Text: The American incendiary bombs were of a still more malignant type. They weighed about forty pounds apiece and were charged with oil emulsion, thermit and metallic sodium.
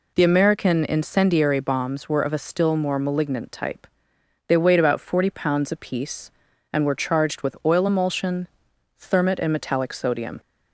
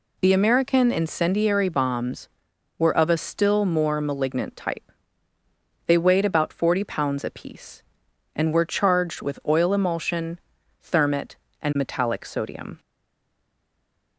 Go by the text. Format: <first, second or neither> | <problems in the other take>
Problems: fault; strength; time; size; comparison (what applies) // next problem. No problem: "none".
first | stays silent after the last word; noticeable; from 12.7 s on; 1.4 s long